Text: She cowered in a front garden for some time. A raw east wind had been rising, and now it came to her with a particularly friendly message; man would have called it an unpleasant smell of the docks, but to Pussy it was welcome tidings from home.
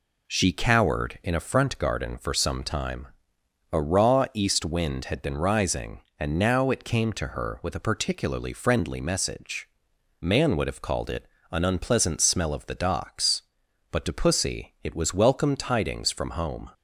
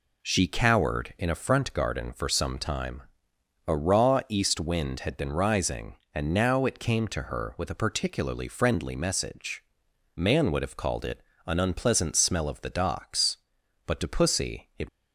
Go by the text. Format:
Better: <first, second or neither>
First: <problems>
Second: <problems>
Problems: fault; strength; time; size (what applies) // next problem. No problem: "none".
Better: first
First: pauses between "it" and "an"; slight; at 11.2 s; 0.24 s long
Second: pauses between "it" and "an"; slight; at 11.2 s; 0.24 s long // stops before "was welcome tidings from home"; at 14.8 s